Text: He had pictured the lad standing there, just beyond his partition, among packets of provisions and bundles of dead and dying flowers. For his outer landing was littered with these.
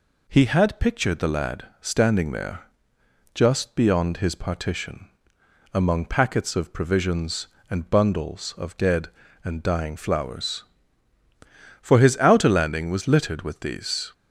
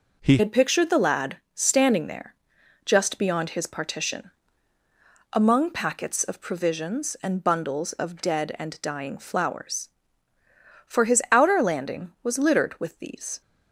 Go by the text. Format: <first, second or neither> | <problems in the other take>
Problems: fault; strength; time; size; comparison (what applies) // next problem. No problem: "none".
first | changes voice at "had"; from 0.3 s on; 13.1 s long // pauses between "lad" and "standing"; slight; at 1.3 s; 0.18 s long